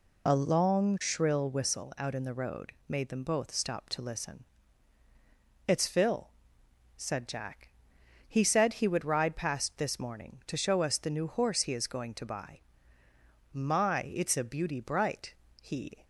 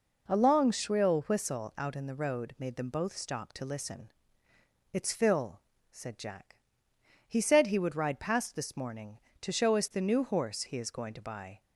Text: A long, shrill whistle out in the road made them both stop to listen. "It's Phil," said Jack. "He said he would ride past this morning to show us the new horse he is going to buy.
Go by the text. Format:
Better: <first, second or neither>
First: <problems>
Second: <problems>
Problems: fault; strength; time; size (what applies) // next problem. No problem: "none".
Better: second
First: goes on to say "My It's a beauty bright he"; strong; from 13.5 s on; 2.5 s long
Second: none